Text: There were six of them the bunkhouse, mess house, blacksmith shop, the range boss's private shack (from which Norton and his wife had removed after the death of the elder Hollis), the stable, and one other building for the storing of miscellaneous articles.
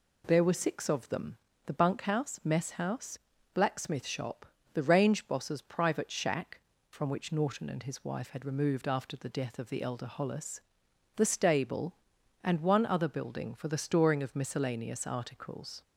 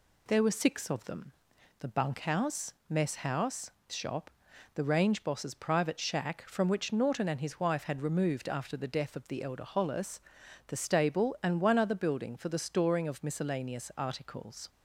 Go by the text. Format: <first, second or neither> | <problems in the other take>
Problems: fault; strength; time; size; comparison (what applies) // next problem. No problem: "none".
first | pauses between "them" and "the"; noticeable; at 1.3 s; 0.48 s long; slight in the first // skips "blacksmith"; at 3.8 s